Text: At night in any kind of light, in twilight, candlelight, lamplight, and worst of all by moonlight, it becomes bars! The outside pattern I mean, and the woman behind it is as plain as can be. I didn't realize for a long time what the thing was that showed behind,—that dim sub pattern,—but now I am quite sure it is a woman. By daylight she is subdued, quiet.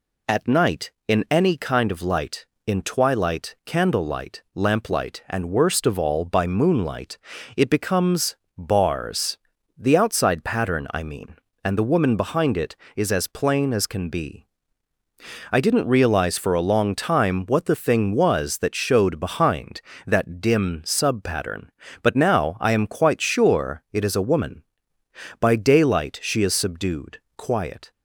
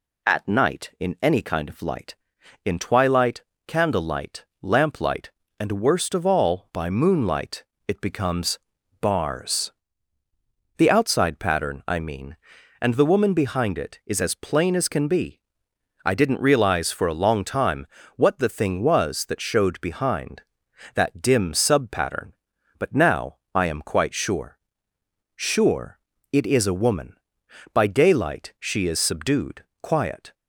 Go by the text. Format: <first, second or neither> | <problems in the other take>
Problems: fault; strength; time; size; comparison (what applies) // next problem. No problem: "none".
first | pauses between "becomes" and "bars"; at 8.5 s; 0.42 s long; slight in the first // pauses between "time" and "what"; slight; at 17.8 s; 0.28 s long // pauses between "now" and "I"; slight; at 23.3 s; 0.16 s long // says "sure" twice; at 25.3 s